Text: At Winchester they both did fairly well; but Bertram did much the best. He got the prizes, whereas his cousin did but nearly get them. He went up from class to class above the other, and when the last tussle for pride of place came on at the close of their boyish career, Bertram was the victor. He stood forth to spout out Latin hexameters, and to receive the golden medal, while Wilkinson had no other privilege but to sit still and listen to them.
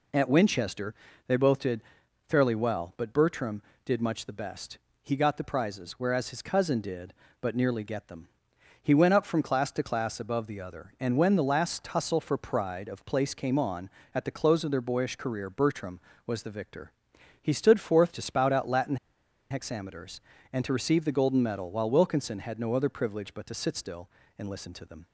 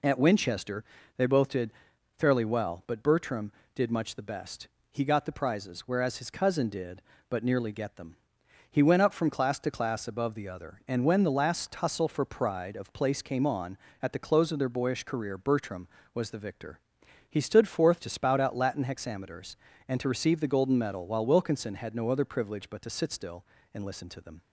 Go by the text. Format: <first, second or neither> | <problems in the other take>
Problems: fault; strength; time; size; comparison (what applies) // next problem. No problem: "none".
second | pauses between "Winchester" and "they"; slight; at 0.9 s; 0.34 s long; slight in the second // pauses between "did" and "fairly"; noticeable; at 1.8 s; 0.46 s long; noticeable in the second // pauses between "Latin" and "hexameters"; noticeable; at 18.9 s; 0.55 s long